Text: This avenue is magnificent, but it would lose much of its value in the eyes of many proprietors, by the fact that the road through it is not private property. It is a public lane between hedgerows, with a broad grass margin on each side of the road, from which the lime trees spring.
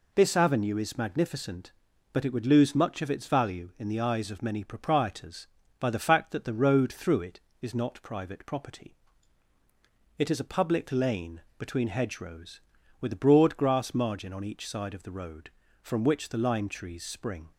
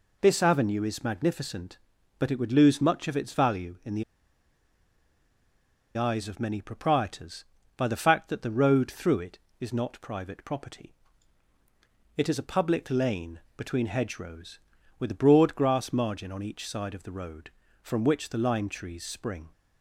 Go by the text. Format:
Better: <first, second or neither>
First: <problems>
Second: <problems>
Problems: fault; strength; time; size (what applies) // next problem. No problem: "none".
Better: first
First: pauses between "lane" and "between"; slight; at 11.4 s; 0.16 s long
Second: pauses between "the" and "eyes"; strong; at 4.0 s; 1.9 s long // pauses between "lane" and "between"; slight; at 13.4 s; 0.16 s long